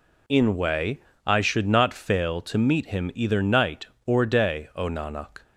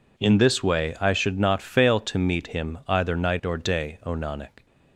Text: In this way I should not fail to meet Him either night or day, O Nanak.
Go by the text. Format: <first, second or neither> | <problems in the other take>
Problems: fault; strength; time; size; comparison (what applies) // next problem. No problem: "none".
second | skips "this"; at 0.5 s // pauses between "way" and "I"; slight; at 0.9 s; 0.26 s long